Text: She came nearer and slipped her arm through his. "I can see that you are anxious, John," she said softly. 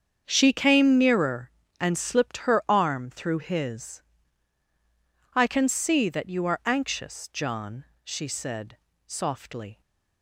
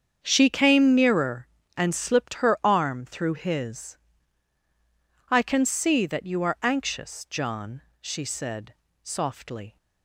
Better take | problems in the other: neither | starts louder than the rest; strong; the same in both // pauses between "said" and "softly"; slight; the same in both

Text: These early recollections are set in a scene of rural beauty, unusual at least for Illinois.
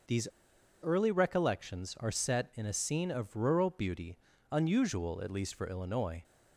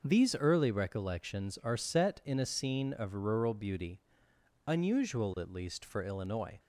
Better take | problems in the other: second | starts louder than the rest; until 1.6 s; 6.5 dB // pauses between "These" and "early"; noticeable; at 0.2 s; 0.55 s long

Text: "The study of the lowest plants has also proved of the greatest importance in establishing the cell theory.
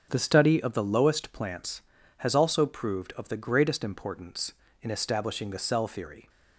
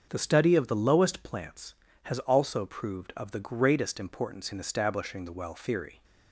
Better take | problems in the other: first | starts louder than the rest; until 1.1 s; 6.5 dB; also in the first // says "well" for "cell"; at 5.3 s

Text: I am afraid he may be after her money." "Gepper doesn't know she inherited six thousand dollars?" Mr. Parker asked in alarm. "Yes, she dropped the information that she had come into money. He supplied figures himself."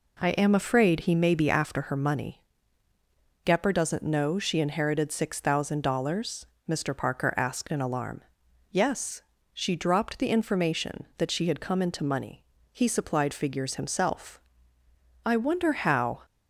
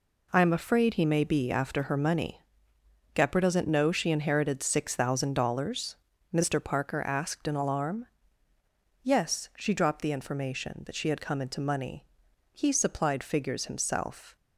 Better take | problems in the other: second | goes on to say "I wonder how"; noticeable; from 15.2 s on; 0.98 s long

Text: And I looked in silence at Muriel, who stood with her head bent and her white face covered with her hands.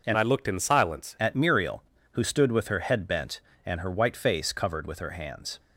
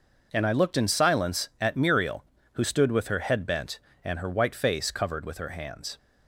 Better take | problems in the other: second | changes voice from "I" to "silence"; from 0.1 to 1.1 s; 1.0 s long

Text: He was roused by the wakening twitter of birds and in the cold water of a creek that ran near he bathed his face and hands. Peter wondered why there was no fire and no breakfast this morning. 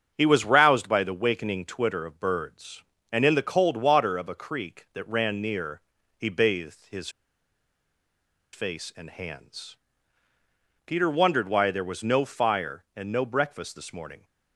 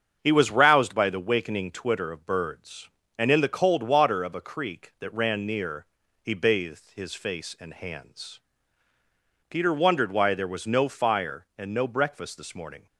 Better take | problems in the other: second | starts louder than the rest; strong; until 1.1 s; 7.5 dB; strong in the second // pauses between "near" and "he"; at 5.8 s; 0.38 s long; also in the second // pauses between "his" and "face"; strong; at 7.0 s; 1.4 s long

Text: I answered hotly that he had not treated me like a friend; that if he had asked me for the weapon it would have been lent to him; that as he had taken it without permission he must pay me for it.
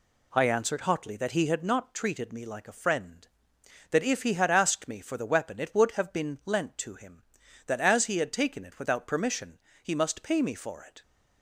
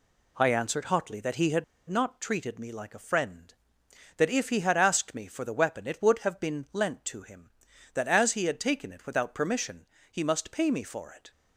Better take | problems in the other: first | pauses between "had" and "not"; slight; at 1.6 s; 0.23 s long // pauses between "permission" and "he"; slight; at 9.8 s; 0.24 s long; slight in the first

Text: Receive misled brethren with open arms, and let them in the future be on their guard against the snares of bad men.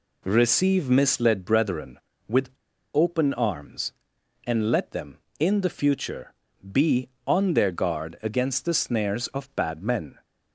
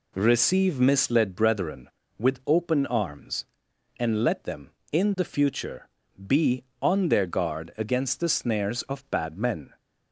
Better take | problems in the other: second | pauses between "with" and "open"; noticeable; at 2.4 s; 0.46 s long // pauses between "future" and "be"; slight; at 6.3 s; 0.28 s long; slight in the second

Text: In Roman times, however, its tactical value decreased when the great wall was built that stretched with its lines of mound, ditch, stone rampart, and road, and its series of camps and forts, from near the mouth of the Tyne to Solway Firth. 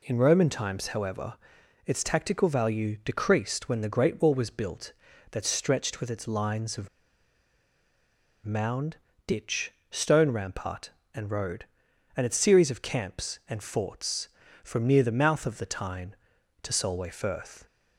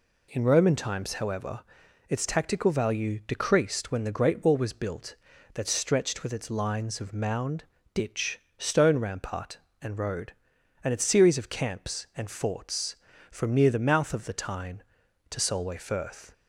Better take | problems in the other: second | pauses between "of" and "mound"; strong; at 6.8 s; 1.5 s long

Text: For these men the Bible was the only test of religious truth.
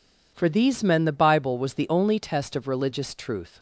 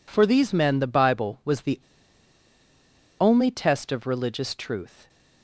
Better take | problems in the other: first | pauses between "the" and "only"; strong; at 1.7 s; 1.4 s long

